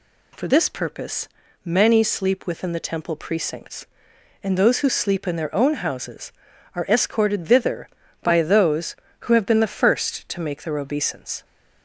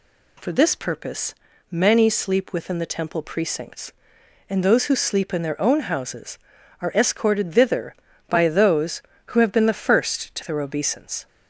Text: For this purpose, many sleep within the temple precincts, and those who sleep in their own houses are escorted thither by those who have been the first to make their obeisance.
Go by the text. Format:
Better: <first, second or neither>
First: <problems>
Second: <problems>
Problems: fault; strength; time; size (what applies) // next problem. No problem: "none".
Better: first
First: none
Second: skips "make"; at 10.4 s